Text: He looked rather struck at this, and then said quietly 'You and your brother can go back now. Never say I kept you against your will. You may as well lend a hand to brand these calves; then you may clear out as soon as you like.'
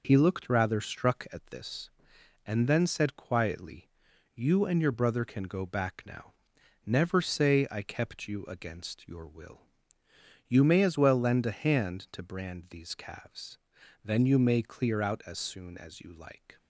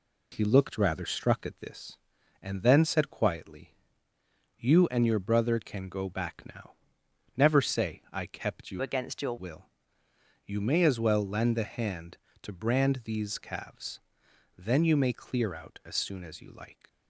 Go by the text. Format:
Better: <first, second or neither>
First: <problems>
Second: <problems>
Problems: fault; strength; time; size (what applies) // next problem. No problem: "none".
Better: first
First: pauses between "quietly" and "You"; noticeable; at 3.8 s; 0.46 s long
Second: pauses between "quietly" and "You"; noticeable; at 3.7 s; 0.82 s long // changes voice from "against" to "your"; from 8.8 to 9.3 s; 0.5 s long